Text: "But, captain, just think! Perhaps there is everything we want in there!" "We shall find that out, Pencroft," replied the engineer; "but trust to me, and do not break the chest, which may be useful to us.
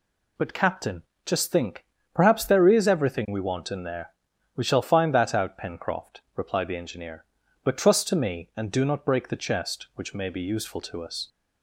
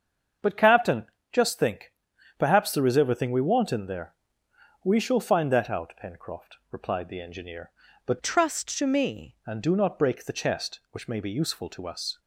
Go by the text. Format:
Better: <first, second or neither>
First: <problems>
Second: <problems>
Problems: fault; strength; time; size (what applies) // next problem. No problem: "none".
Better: first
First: none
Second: starts louder than the rest; strong; until 1.6 s; 7 dB // changes voice from "trust" to "me"; from 8.2 to 9.3 s; 1.1 s long